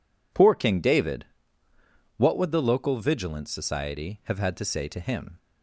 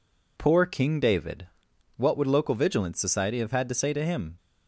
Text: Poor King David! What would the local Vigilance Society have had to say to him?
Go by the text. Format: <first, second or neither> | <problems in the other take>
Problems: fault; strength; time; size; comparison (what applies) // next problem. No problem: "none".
first | skips "the"; at 2.2 s